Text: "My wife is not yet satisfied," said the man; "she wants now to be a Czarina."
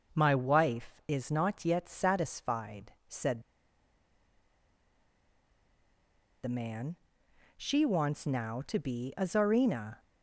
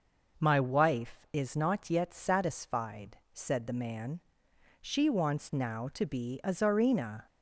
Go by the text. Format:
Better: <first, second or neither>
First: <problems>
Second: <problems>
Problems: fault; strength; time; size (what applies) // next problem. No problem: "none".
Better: second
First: pauses between "said" and "the"; strong; at 3.4 s; 3.0 s long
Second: none